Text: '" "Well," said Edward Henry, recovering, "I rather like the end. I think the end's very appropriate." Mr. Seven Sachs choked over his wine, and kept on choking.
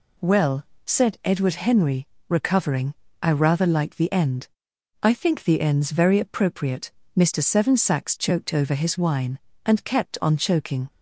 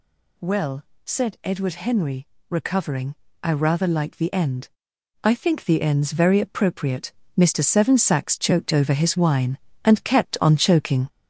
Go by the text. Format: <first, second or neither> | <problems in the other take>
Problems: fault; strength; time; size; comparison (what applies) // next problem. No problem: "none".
first | gets louder; noticeable; throughout; 5.5 dB